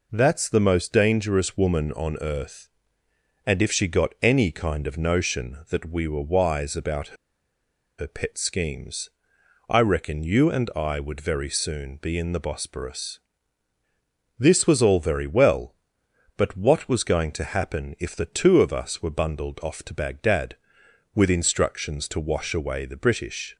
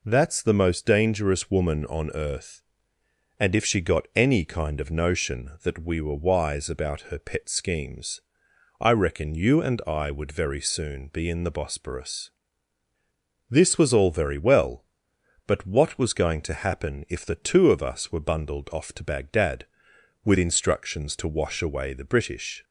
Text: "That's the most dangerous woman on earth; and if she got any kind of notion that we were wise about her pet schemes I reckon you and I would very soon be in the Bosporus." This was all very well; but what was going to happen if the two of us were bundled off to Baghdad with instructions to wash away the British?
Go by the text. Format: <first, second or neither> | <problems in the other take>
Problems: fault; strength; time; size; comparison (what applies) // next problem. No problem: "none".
second | pauses between "about" and "her"; noticeable; at 7.1 s; 0.84 s long // pauses between "schemes" and "I"; noticeable; at 9.0 s; 0.58 s long; noticeable in the second